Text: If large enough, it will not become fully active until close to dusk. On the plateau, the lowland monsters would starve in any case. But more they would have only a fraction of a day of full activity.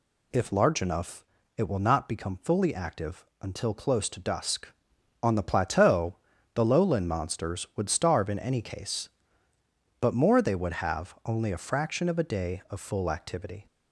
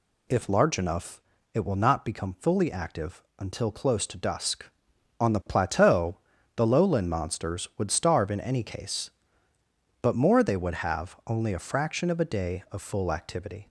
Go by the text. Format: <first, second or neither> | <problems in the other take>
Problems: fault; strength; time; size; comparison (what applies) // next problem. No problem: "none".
neither | pauses between "active" and "until"; slight; the same in both